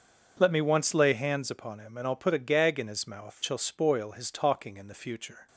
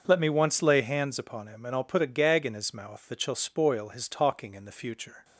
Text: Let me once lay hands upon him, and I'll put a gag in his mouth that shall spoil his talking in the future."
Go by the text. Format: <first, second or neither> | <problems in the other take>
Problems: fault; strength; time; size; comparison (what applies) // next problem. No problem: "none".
second | starts louder than the rest; until 1.4 s; 6.5 dB; also in the second // skips "that"; at 3.4 s